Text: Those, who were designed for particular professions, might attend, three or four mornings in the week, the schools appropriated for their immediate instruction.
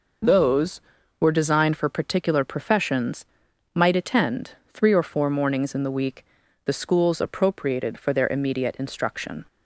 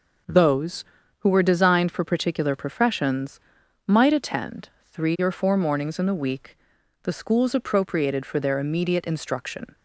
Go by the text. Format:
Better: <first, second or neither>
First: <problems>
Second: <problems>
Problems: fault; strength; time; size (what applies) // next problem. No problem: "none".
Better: second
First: skips "who"; at 0.9 s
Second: none